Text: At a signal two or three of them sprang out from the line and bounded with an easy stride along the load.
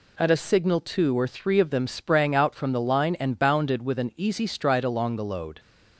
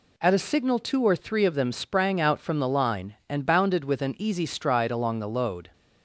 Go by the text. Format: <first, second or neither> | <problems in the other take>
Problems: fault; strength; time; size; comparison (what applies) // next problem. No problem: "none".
neither | none